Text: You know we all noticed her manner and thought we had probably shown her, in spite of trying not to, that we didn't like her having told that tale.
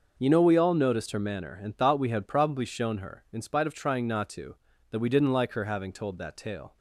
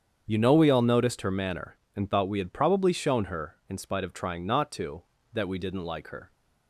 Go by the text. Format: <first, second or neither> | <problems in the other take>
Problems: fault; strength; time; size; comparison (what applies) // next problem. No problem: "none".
first | starts louder than the rest; strong; until 1.2 s; 8 dB; noticeable in the first // stops before "having told that tale"; at 6.3 s